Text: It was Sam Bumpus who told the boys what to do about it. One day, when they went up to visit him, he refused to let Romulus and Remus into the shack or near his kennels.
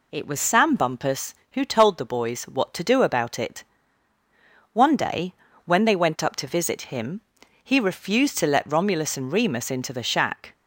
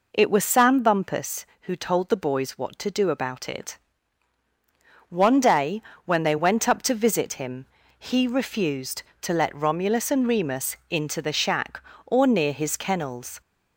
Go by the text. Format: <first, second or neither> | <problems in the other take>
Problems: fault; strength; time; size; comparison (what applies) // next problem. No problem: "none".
second | stops before "or near his kennels"; at 10.5 s